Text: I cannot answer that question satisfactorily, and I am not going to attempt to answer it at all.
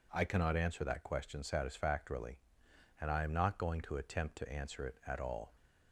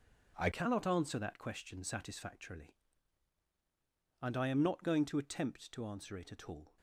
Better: first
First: none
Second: changes voice at "cannot"; from 0.5 s on; 6.2 s long

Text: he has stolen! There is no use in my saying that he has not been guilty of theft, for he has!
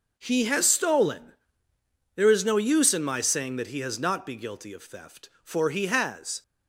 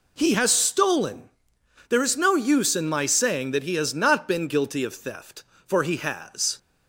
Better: second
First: says "be" for "been"; at 4.2 s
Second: none

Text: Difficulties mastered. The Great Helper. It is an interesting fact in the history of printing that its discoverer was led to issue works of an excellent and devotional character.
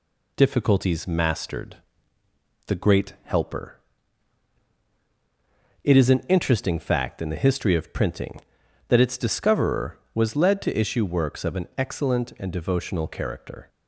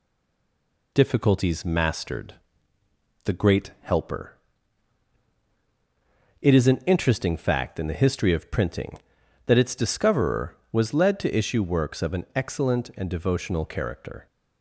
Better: first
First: none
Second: stays silent before the first word; slight; until 0.9 s; 0.9 s long

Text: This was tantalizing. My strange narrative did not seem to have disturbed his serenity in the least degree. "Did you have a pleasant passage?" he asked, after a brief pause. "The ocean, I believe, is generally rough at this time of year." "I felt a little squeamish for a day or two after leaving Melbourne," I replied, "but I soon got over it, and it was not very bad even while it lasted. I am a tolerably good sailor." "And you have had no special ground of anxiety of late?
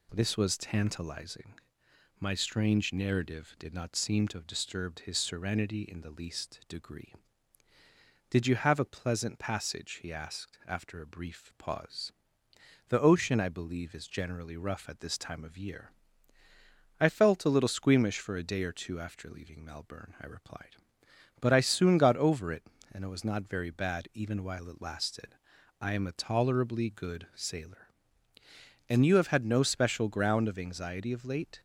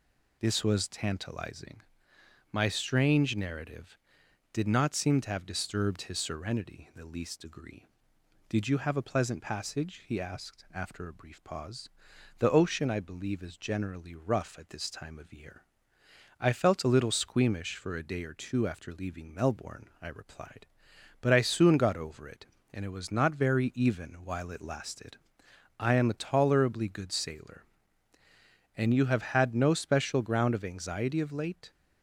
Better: first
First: none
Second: skips "bad"; at 23.7 s

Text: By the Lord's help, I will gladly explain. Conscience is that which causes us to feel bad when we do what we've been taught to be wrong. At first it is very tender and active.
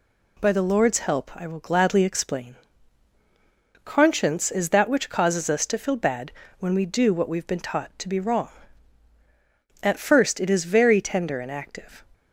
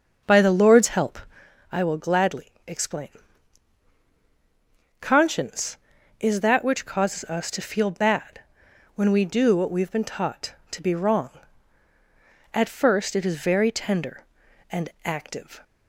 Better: first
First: pauses between "bad" and "when"; slight; at 6.2 s; 0.30 s long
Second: starts louder than the rest; until 1.5 s; 6 dB // pauses between "bad" and "when"; noticeable; at 8.3 s; 0.56 s long

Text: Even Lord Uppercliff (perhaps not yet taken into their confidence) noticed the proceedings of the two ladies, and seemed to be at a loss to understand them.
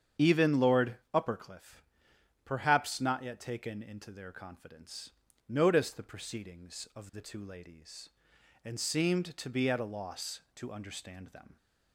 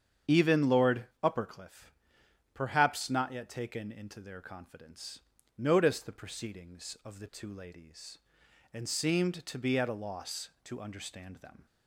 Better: neither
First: starts louder than the rest; strong; until 1.3 s; 8 dB // pauses between "Lord" and "Uppercliff"; slight; at 0.9 s; 0.18 s long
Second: starts louder than the rest; strong; until 1.4 s; 7.5 dB // pauses between "Lord" and "Uppercliff"; slight; at 1.0 s; 0.18 s long

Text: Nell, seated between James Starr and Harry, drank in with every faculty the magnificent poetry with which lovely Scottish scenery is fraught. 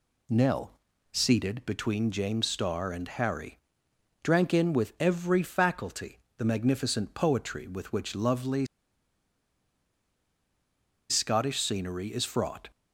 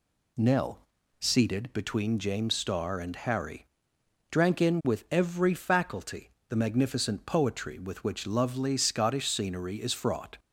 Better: second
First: pauses between "faculty" and "the"; slight; at 6.1 s; 0.20 s long // pauses between "lovely" and "Scottish"; strong; at 8.6 s; 2.4 s long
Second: pauses between "faculty" and "the"; slight; at 6.2 s; 0.20 s long

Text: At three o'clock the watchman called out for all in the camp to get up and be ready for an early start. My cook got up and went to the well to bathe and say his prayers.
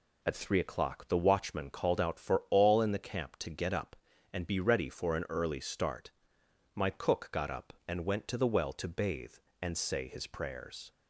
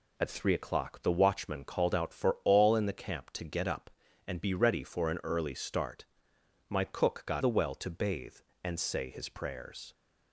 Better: first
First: none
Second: skips "up and went to"; at 7.4 s

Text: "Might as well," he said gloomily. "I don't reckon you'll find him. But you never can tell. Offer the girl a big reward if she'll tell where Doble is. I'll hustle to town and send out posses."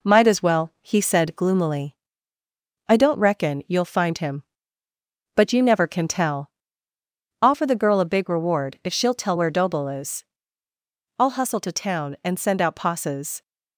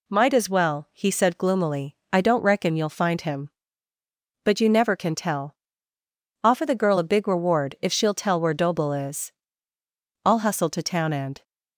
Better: first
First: none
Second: stops before "send out posses"; at 11.4 s

